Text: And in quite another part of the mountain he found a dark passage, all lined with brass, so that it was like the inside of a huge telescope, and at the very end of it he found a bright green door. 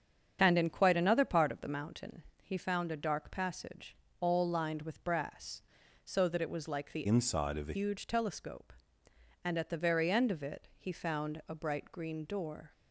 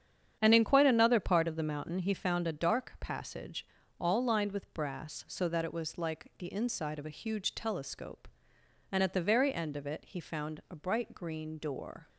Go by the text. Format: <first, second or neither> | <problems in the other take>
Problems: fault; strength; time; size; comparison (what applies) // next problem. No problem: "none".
second | starts louder than the rest; strong; until 1.4 s; 8 dB; strong in the second // pauses between "mountain" and "he"; slight; at 2.2 s; 0.20 s long // changes voice from "inside" to "a"; from 7.0 to 7.7 s; 0.7 s long